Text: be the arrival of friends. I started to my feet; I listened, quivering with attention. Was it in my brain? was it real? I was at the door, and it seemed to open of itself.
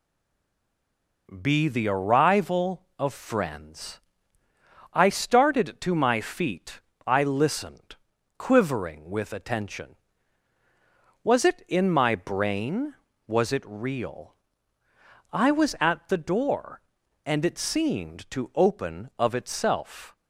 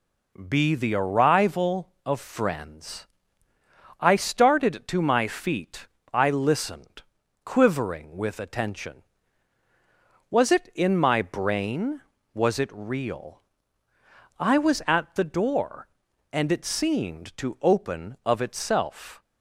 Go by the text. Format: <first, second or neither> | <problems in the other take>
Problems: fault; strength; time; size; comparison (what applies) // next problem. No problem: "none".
second | stays silent before the first word; noticeable; until 1.2 s; 1.2 s long